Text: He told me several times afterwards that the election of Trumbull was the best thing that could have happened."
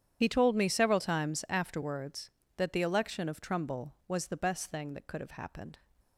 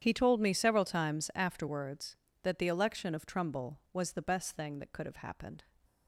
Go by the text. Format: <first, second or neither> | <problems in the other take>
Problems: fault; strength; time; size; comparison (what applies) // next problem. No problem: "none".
second | loses the start of "He"; at 0.2 s; 35 ms // starts louder than the rest; strong; until 1.2 s; 9 dB; strong in the second